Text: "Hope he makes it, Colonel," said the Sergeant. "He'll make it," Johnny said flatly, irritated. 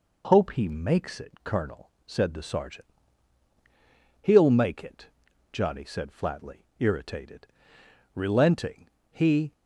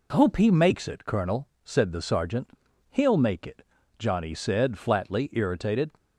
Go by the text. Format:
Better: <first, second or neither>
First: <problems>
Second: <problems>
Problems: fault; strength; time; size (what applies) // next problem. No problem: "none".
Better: second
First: goes on to say "Relenting he"; from 8.1 s on; 1.4 s long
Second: none